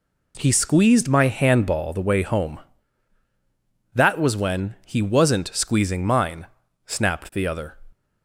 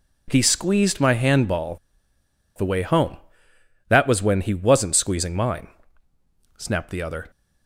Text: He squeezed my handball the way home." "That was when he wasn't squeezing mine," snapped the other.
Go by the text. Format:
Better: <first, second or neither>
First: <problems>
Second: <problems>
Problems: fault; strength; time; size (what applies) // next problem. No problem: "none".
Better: first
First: none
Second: pauses between "handball" and "the"; noticeable; at 1.7 s; 0.81 s long